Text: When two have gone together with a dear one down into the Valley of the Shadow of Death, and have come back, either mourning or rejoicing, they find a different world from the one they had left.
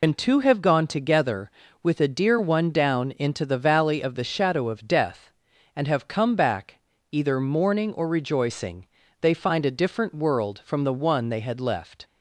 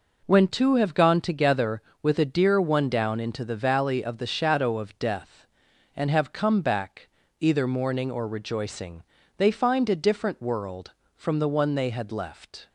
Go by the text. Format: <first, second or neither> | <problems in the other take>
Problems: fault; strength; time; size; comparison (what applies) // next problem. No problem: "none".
second | loses the start of "When"; at 0.0 s; 85 ms